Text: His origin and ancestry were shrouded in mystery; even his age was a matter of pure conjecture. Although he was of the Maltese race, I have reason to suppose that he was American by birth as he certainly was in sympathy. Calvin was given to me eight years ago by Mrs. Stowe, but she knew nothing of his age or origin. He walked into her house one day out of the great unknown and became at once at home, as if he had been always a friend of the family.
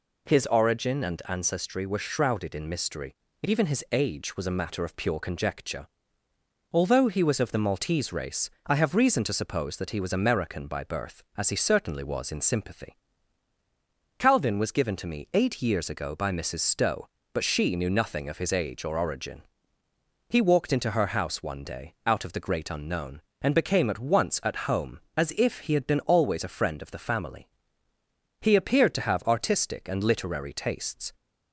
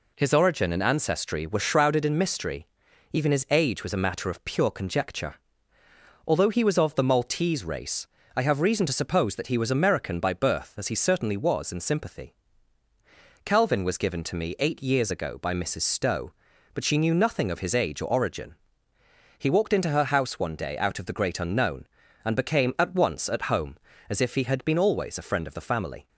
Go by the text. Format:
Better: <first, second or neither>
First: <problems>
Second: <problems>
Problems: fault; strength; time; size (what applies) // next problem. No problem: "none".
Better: second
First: goes on to say "He appeared to have artistic and literary tastes"; strong; from 28.4 s on; 2.7 s long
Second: none